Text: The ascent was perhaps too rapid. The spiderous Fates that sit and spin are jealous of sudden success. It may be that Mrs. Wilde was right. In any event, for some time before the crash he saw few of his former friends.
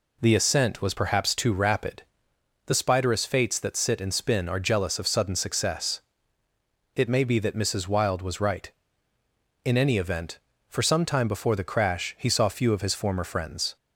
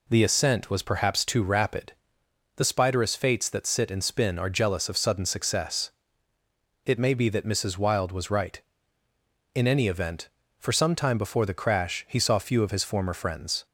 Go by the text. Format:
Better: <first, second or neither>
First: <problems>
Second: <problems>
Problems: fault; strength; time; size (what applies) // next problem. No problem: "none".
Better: neither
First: none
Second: none